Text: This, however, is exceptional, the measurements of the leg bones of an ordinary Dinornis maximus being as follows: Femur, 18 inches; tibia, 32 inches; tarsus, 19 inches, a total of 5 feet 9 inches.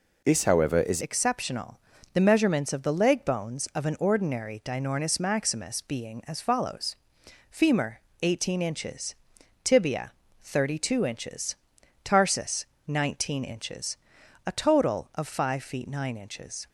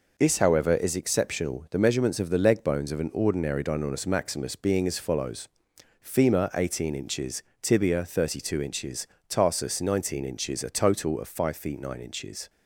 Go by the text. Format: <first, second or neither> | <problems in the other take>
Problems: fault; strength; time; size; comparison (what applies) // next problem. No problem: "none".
second | changes voice at "exceptional"; from 1.0 s on; 15.6 s long